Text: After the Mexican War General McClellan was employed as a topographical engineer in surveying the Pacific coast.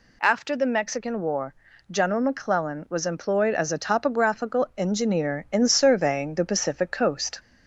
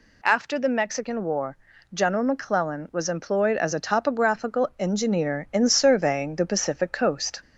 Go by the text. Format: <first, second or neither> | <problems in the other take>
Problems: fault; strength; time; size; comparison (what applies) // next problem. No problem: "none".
neither | pauses between "War" and "General"; slight; the same in both